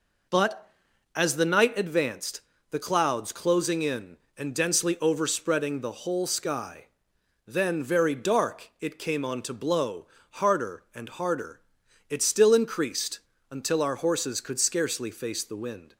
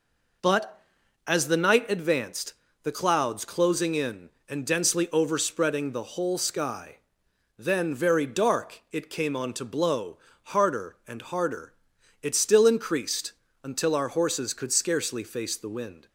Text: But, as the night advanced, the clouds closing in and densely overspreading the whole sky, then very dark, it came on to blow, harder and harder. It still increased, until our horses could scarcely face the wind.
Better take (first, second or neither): neither